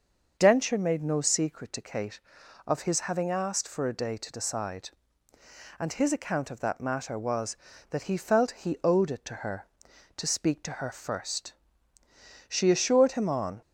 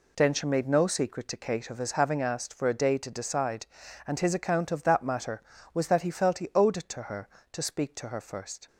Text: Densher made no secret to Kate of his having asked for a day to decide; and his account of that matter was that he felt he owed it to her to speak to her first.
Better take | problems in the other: second | starts louder than the rest; until 1.3 s; 6 dB // goes on to say "She assured him on"; noticeable; from 12.4 s on; 1.1 s long

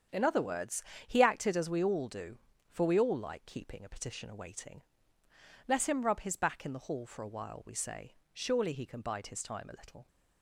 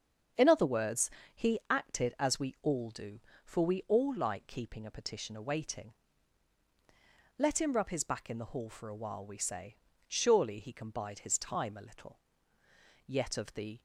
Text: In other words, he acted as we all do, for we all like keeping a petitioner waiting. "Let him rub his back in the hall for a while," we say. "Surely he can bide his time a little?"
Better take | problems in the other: first | starts louder than the rest; strong; until 1.7 s; 7 dB; strong in the first // goes on to say "Yet of the"; noticeable; from 13.0 s on; 0.74 s long

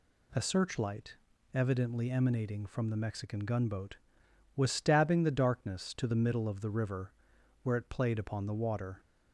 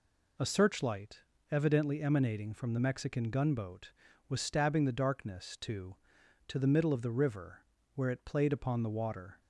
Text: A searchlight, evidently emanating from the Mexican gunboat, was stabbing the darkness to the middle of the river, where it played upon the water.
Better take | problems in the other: first | says "to" twice; at 6.4 s

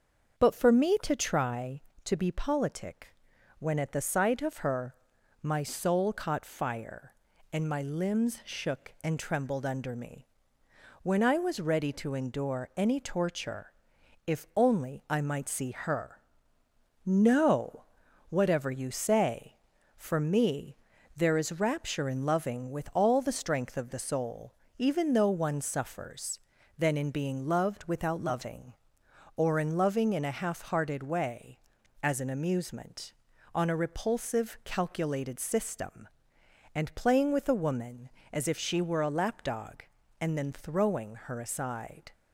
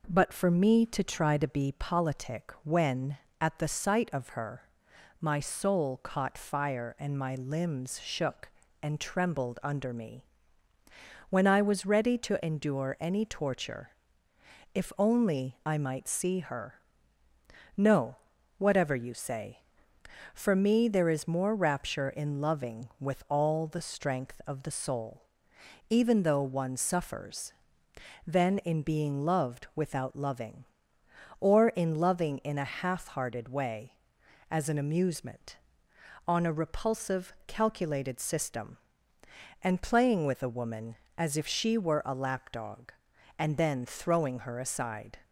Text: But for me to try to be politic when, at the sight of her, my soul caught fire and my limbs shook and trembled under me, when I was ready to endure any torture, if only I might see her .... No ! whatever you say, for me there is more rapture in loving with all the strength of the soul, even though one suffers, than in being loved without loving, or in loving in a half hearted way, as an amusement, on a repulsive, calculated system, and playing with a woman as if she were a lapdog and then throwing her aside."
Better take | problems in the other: second | starts louder than the rest; until 1.4 s; 7 dB // pauses between "politic" and "when"; at 3.1 s; 0.44 s long // pauses between "me" and "there"; at 20.7 s; 0.40 s long // skips "more"; at 21.6 s

